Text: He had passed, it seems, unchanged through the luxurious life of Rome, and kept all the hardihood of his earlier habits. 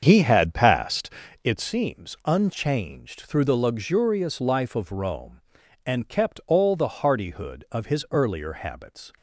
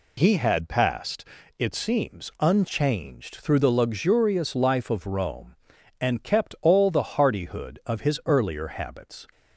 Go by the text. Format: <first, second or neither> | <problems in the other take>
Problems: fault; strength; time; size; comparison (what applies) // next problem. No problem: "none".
second | starts louder than the rest; strong; until 1.7 s; 7 dB